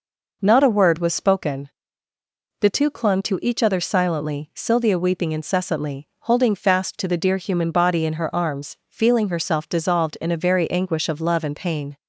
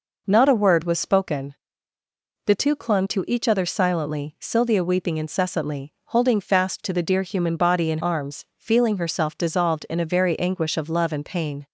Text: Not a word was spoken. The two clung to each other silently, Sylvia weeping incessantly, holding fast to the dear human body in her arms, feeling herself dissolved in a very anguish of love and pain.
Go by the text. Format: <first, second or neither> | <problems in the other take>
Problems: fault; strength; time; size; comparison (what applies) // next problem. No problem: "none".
first | skips "her"; at 7.9 s